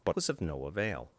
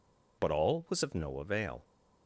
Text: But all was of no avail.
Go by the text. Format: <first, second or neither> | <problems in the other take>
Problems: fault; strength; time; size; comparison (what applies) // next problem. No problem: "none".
second | skips "all"; at 0.1 s